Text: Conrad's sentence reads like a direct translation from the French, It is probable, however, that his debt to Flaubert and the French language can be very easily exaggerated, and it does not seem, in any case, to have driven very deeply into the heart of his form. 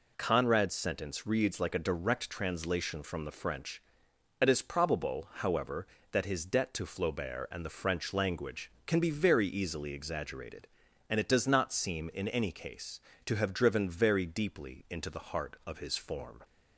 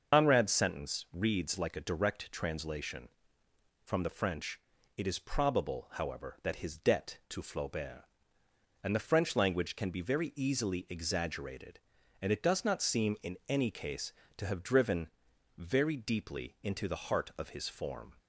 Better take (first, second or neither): first